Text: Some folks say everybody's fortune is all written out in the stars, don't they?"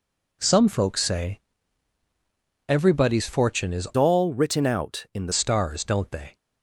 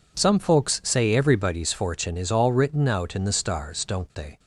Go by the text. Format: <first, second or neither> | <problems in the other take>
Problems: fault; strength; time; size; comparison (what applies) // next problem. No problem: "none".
second | pauses between "say" and "everybody's"; at 1.4 s; 1.2 s long // changes voice from "all" to "the"; from 3.9 to 5.3 s; 1.4 s long